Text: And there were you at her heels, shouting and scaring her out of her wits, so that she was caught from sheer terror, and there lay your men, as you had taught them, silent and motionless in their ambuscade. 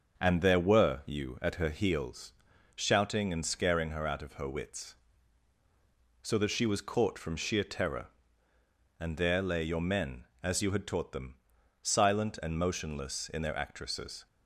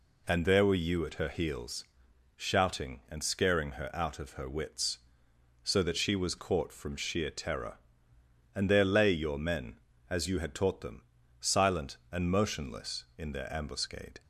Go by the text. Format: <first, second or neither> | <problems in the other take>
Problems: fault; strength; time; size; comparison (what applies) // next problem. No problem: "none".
second | starts louder than the rest; until 1.2 s; 6.5 dB // says "actresses" for "ambuscade"; at 13.5 s